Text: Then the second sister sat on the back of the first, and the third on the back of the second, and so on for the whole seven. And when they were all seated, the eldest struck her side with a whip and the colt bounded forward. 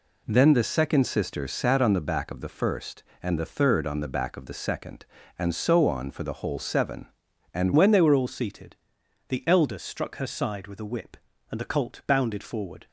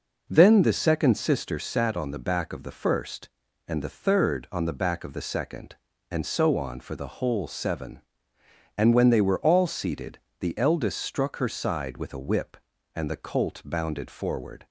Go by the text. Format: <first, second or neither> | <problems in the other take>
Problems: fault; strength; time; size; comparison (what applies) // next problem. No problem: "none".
second | changes voice at "when"; from 7.7 s on; 5.1 s long